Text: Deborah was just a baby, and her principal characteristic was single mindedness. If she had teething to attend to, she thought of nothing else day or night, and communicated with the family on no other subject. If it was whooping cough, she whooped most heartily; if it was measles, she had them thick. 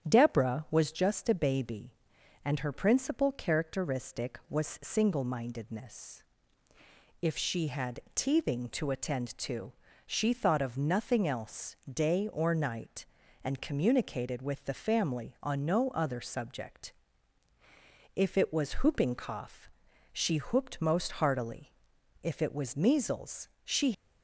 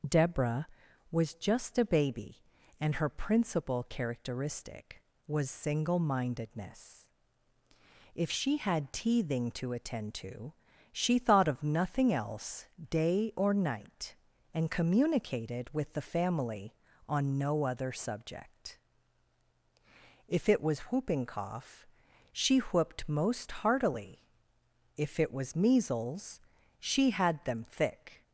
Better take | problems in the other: second | starts louder than the rest; strong; until 1.1 s; 9 dB // pauses between "else" and "day"; slight; at 11.7 s; 0.16 s long; slight in the second // stops before "had them thick"; at 23.9 s

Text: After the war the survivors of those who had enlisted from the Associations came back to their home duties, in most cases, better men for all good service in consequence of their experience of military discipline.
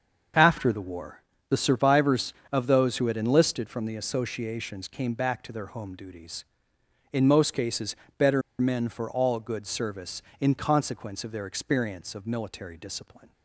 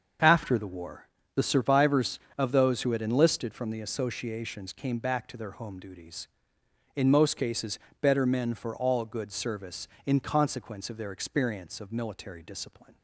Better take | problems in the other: second | starts louder than the rest; until 1.6 s; 6.5 dB; also in the second // pauses between "war" and "the"; slight; at 1.2 s; 0.28 s long; slight in the second // pauses between "better" and "men"; slight; at 8.4 s; 0.19 s long

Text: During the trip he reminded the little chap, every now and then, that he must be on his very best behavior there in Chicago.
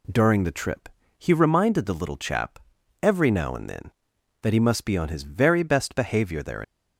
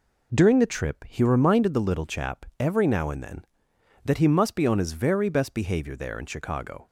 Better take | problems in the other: second | pauses between "trip" and "he"; slight; at 0.8 s; 0.30 s long // stops before "in Chicago"; at 6.6 s

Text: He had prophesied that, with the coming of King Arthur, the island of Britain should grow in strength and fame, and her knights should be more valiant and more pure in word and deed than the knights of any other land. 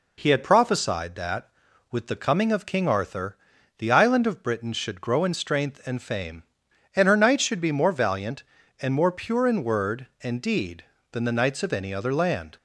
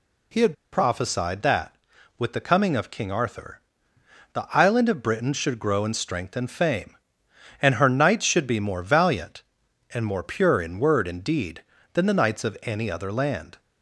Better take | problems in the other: first | pauses between "had" and "prophesied"; slight; at 0.5 s; 0.18 s long

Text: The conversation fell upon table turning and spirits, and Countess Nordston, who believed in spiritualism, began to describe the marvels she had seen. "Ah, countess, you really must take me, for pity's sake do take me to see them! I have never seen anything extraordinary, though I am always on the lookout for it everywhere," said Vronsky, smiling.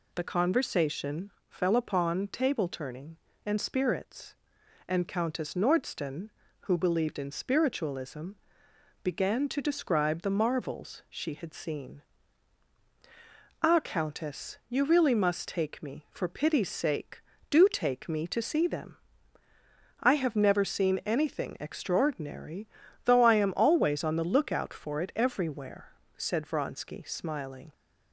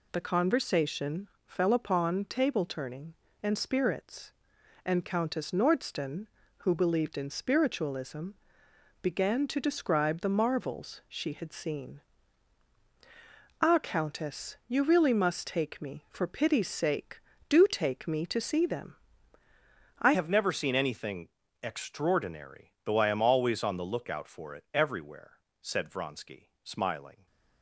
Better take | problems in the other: first | pauses between "conversation" and "fell"; slight; at 1.2 s; 0.16 s long; slight in the first // changes voice at "have"; from 20.1 s on; 7.1 s long // pauses between "anything" and "extraordinary"; slight; at 21.2 s; 0.34 s long

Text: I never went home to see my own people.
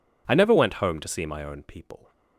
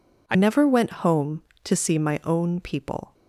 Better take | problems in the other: first | changes voice at "never"; from 0.3 s on; 2.8 s long

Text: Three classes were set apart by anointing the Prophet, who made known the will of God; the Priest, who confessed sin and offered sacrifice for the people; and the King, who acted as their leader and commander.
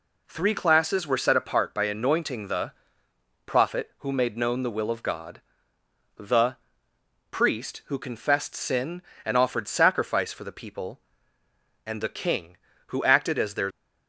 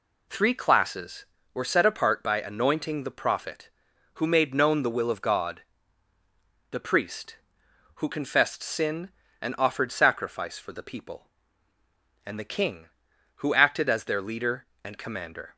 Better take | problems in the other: second | pauses between "the" and "Prophet"; noticeable; at 2.7 s; 0.74 s long // pauses between "the" and "Priest"; noticeable; at 6.5 s; 0.74 s long // stops before "leader and commander"; at 13.7 s

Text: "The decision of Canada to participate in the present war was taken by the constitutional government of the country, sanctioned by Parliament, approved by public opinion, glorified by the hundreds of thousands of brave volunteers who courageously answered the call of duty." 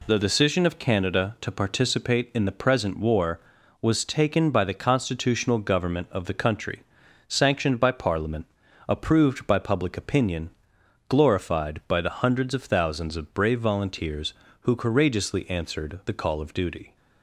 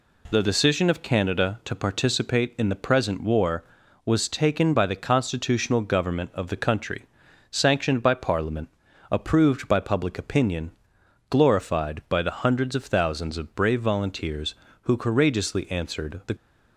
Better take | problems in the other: first | stops before "call of duty"; at 16.3 s

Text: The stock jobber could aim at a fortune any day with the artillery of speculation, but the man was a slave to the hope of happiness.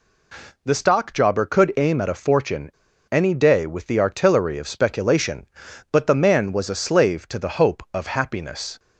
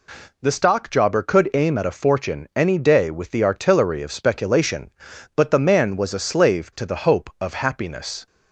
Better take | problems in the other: second | pauses between "fortune" and "any"; at 2.7 s; 0.40 s long

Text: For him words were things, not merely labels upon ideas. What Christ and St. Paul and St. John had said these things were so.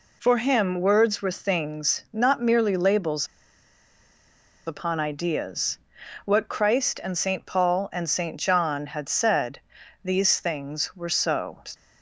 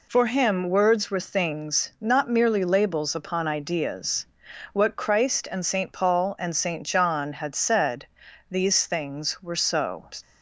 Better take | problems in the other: second | pauses between "labels" and "upon"; strong; at 3.2 s; 1.4 s long // pauses between "said" and "these"; at 9.5 s; 0.42 s long; also in the second

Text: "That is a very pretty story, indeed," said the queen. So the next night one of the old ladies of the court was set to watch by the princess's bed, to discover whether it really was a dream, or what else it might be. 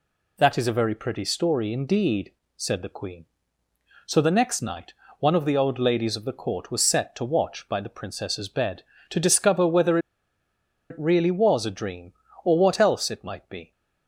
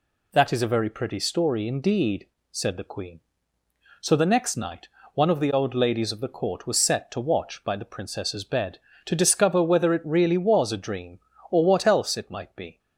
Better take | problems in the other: second | pauses between "night" and "one"; slight; at 4.9 s; 0.26 s long; slight in the second // pauses between "whether" and "it"; noticeable; at 9.9 s; 0.92 s long

